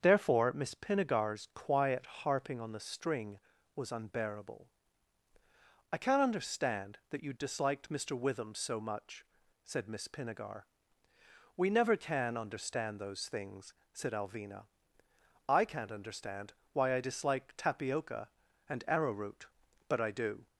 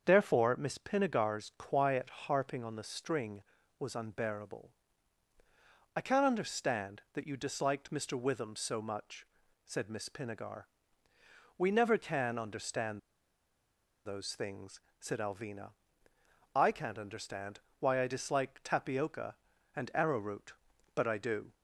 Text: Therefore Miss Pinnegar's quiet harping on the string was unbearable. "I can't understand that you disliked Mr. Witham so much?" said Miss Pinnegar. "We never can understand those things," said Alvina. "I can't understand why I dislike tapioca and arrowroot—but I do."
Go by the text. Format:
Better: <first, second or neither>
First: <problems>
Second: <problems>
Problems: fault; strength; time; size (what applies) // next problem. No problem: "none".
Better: first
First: starts louder than the rest; until 1.0 s; 7 dB // pauses between "understand" and "why"; slight; at 16.5 s; 0.20 s long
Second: starts louder than the rest; until 1.0 s; 7 dB // pauses between "understand" and "those"; at 12.9 s; 1.0 s long // pauses between "understand" and "why"; slight; at 17.5 s; 0.20 s long